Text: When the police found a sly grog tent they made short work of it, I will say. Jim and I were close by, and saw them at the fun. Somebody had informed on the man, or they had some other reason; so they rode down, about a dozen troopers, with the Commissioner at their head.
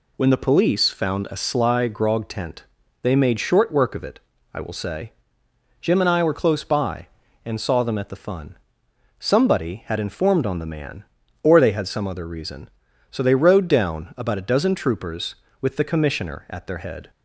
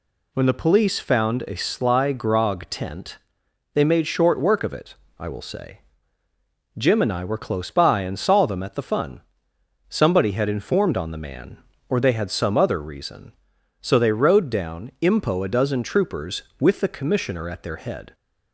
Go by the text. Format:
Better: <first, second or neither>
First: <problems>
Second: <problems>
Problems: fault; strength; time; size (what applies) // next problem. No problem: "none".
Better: first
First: pauses between "tent" and "they"; at 2.6 s; 0.38 s long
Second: pauses between "tent" and "they"; noticeable; at 3.1 s; 0.56 s long // says "impo" for "about"; at 15.0 s